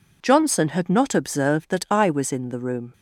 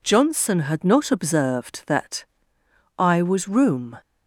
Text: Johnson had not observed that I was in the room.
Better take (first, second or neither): first